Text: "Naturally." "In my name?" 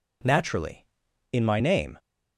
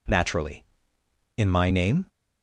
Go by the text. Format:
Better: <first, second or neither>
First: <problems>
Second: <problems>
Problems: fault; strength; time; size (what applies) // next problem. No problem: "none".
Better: neither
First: none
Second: none